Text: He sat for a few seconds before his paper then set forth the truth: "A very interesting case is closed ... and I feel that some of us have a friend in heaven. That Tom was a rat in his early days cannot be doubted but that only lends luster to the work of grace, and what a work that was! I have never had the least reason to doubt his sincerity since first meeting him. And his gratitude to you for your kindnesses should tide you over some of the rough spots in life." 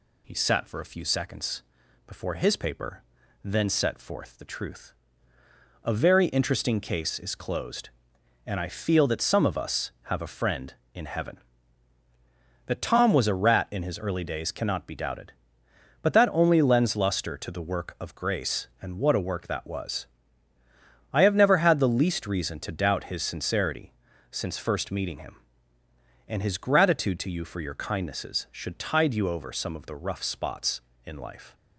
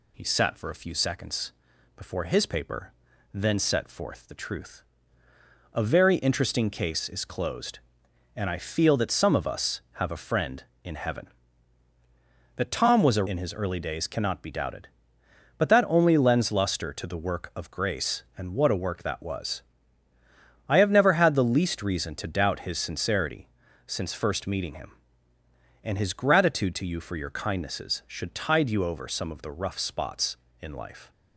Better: first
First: pauses between "seconds" and "before"; noticeable; at 1.6 s; 0.46 s long // pauses between "paper" and "then"; at 3.0 s; 0.40 s long // pauses between "sincerity" and "since"; at 23.9 s; 0.38 s long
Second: pauses between "seconds" and "before"; noticeable; at 1.5 s; 0.46 s long // pauses between "paper" and "then"; at 2.9 s; 0.40 s long // skips "rat"; at 13.2 s // pauses between "sincerity" and "since"; at 23.4 s; 0.38 s long

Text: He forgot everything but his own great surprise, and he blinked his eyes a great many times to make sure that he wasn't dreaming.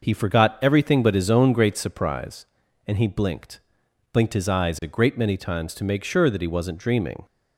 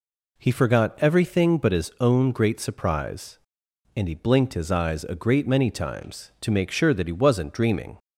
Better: second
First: says "blinked" twice; at 4.1 s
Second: none

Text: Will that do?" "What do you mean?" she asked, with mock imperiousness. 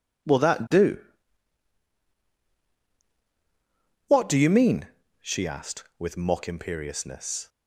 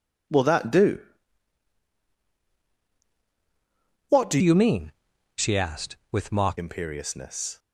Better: first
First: none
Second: changes voice from "you" to "mock"; from 4.4 to 6.5 s; 2.1 s long

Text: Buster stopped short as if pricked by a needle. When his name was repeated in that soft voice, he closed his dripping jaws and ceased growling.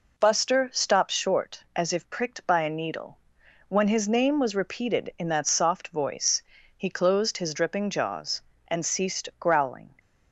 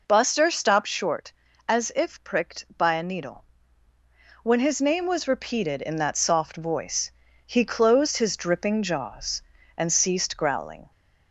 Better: neither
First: none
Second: none

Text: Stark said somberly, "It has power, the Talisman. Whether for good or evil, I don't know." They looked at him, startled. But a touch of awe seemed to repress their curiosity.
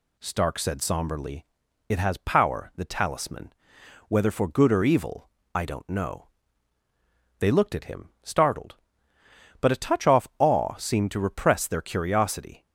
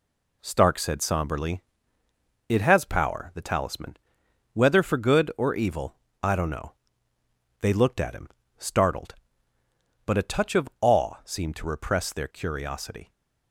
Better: second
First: says "off" for "of"; at 10.0 s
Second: none

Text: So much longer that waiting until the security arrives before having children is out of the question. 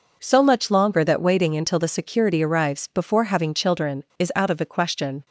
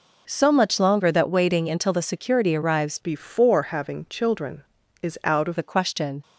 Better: first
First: none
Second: changes voice from "before" to "of"; from 3.0 to 5.5 s; 2.5 s long

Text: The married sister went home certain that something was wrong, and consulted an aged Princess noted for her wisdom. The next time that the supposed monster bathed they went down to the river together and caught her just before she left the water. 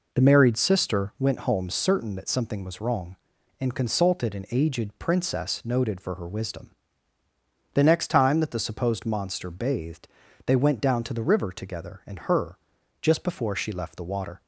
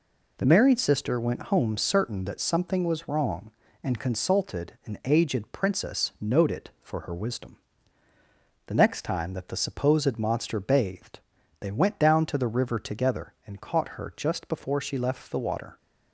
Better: second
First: pauses between "bathed" and "they"; at 10.0 s; 0.38 s long // skips "caught"; at 12.1 s // pauses between "her" and "just"; at 12.5 s; 0.42 s long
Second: pauses between "bathed" and "they"; at 11.1 s; 0.42 s long

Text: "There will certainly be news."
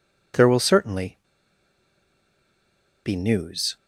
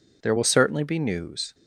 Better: second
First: pauses between "certainly" and "be"; strong; at 1.1 s; 1.8 s long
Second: none

